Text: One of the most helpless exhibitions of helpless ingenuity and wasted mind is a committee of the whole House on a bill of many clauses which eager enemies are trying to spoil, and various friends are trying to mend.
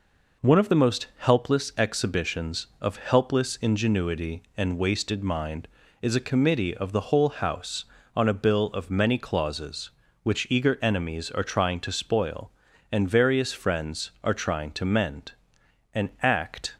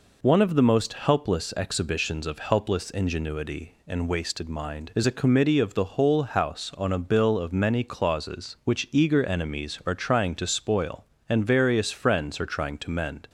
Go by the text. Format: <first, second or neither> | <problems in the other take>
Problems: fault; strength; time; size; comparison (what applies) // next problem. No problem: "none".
second | goes on to say "An Act"; noticeable; from 15.9 s on; 0.82 s long